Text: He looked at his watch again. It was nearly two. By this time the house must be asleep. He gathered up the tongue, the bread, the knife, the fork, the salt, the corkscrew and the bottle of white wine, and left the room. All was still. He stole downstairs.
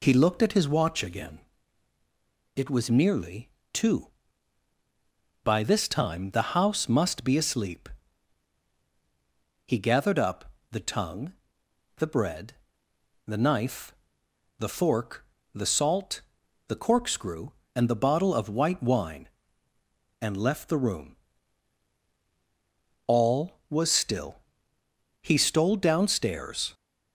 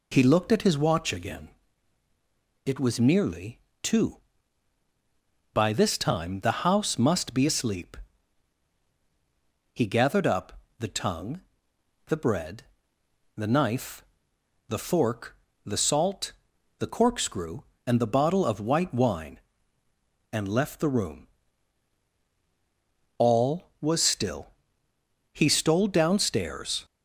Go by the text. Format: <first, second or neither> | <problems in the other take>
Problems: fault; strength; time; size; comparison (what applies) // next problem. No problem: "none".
neither | pauses between "nearly" and "two"; slight; the same in both // pauses between "up" and "the"; slight; the same in both